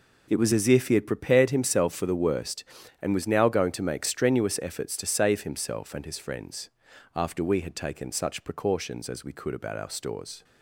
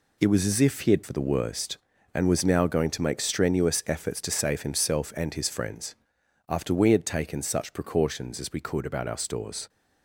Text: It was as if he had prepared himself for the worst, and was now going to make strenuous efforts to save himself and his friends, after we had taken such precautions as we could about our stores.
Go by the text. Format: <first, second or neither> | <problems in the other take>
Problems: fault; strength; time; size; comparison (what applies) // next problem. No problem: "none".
first | skips "prepared himself"; at 1.0 s